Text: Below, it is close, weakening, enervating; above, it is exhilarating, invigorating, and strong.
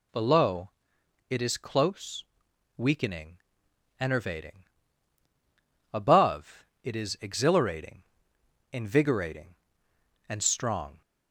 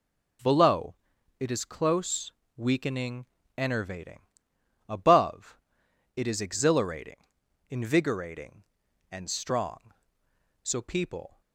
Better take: first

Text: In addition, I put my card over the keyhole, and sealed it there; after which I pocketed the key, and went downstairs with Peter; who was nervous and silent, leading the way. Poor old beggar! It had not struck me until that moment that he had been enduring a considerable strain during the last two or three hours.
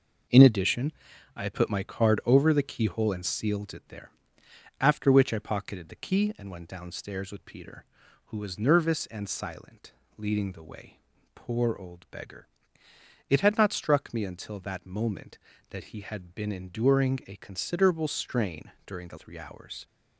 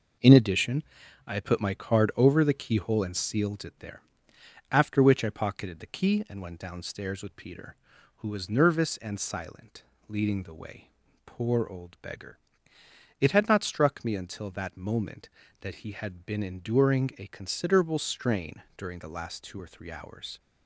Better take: second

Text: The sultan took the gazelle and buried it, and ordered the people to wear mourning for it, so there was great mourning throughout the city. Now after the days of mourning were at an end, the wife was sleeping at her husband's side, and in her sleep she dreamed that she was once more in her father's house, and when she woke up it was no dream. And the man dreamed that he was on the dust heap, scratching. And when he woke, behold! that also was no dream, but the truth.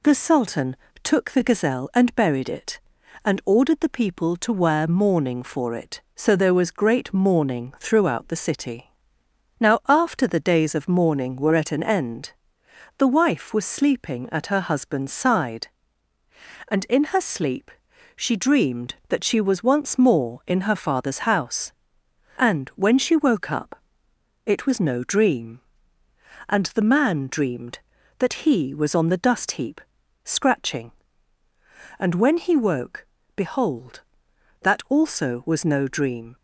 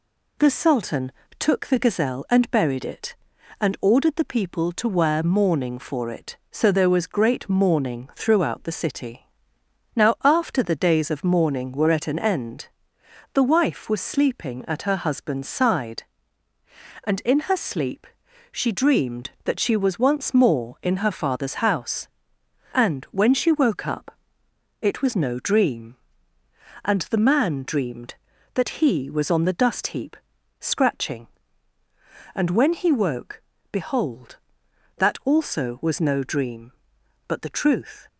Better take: second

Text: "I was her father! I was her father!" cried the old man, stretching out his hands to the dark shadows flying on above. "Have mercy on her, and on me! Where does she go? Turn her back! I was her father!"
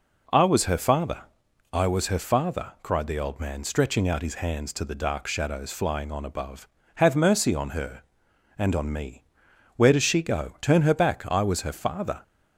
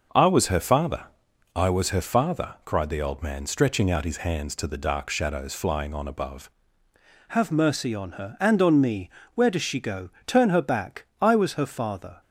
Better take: first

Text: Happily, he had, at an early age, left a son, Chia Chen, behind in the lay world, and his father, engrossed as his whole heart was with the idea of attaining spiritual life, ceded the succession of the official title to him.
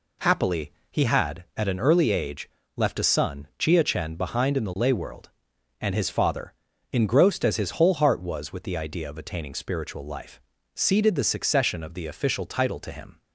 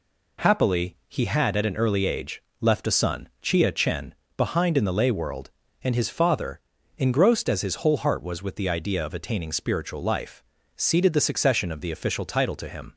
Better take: neither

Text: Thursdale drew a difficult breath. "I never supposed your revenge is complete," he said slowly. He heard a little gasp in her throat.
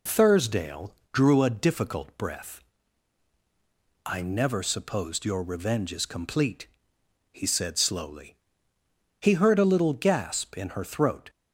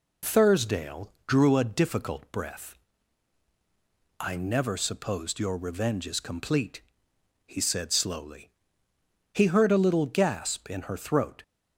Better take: neither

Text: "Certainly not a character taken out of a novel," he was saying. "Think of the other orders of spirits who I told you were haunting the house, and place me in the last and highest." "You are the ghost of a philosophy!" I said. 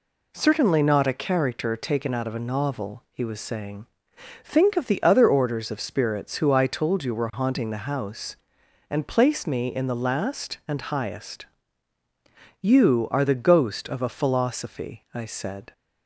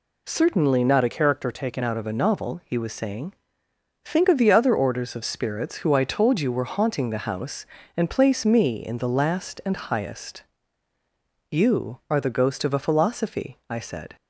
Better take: first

